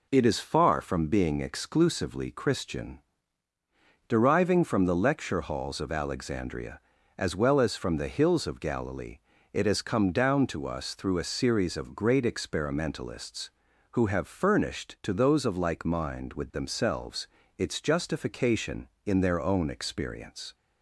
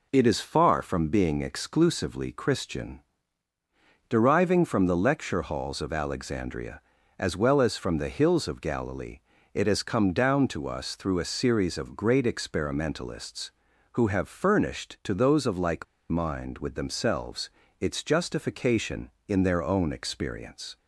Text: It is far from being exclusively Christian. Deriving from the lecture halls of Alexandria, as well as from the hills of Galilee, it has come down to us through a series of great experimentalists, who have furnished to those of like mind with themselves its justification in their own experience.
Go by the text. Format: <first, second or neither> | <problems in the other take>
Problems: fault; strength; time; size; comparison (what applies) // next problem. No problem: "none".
first | pauses between "like" and "mind"; slight; at 15.8 s; 0.24 s long // pauses between "themselves" and "its"; slight; at 17.5 s; 0.28 s long; slight in the first